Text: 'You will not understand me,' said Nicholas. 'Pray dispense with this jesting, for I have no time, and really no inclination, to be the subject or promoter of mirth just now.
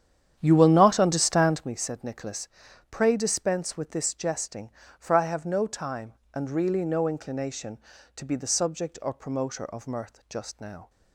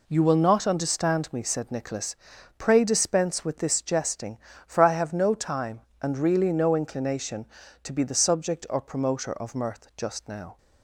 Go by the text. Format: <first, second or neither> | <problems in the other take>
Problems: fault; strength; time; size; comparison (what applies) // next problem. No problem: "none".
second | starts louder than the rest; strong; until 1.8 s; 9.5 dB